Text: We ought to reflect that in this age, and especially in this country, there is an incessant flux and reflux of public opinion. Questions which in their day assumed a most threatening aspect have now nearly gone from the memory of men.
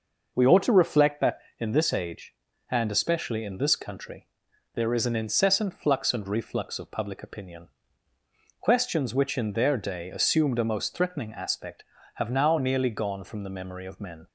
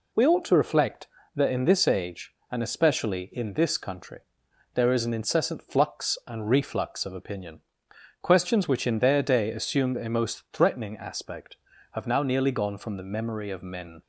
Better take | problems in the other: first | skips "public"; at 7.1 s

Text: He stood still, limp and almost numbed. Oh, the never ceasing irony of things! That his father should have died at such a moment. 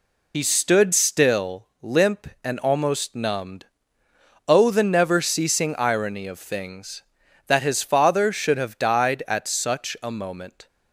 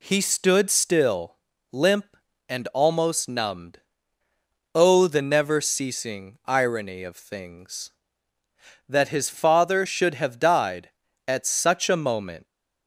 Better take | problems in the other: second | loses the start of "He"; at 0.3 s; 65 ms

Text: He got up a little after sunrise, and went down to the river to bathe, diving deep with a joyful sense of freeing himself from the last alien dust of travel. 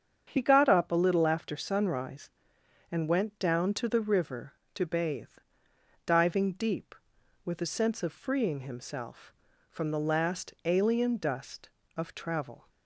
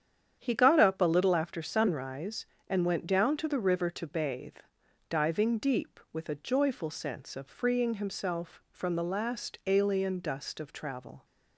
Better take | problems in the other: second | starts louder than the rest; strong; until 1.2 s; 7 dB; strong in the second // skips "joyful"; at 7.6 s

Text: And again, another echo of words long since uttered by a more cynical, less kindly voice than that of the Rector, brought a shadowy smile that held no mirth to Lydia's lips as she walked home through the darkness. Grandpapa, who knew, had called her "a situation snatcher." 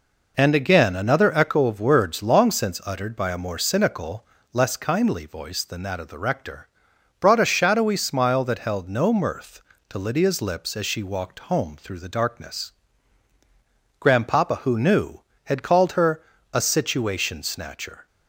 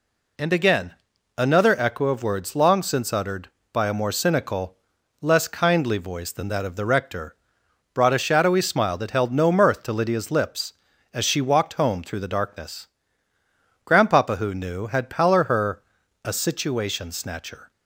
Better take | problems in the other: first | says "pallor" for "called"; at 15.0 s // pauses between "her" and "a"; at 15.8 s; 0.42 s long; slight in the first

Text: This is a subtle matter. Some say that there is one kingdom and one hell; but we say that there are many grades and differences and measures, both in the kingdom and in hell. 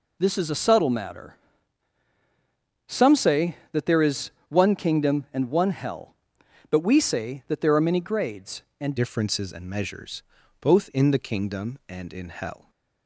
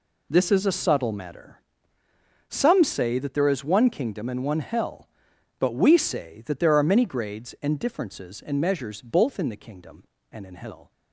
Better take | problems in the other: second | pauses between "is" and "one"; slight; at 4.3 s; 0.16 s long // changes voice at "differences"; from 8.9 s on; 3.7 s long

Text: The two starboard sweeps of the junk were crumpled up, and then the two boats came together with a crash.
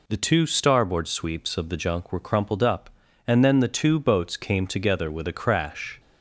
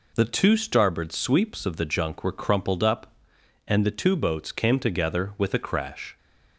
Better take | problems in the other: first | skips "then"; at 3.8 s

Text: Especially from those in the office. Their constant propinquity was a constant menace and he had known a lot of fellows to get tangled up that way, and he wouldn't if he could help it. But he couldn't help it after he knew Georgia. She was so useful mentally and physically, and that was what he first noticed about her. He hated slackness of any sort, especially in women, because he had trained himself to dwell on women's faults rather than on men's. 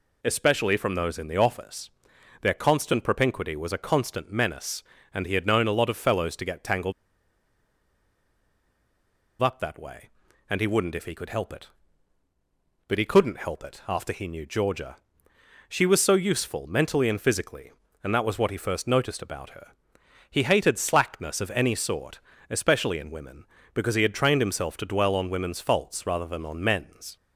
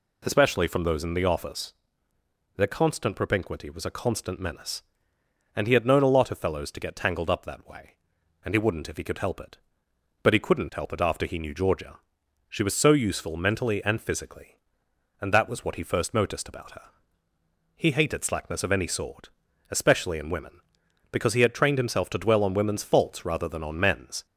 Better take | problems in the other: second | pauses between "tangled" and "up"; strong; at 6.9 s; 2.4 s long

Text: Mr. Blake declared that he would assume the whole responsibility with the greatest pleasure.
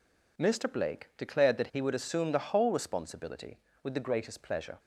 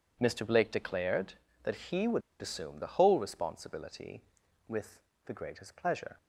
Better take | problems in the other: first | pauses between "would" and "assume"; slight; at 2.2 s; 0.19 s long // pauses between "with" and "the"; slight; at 4.9 s; 0.26 s long

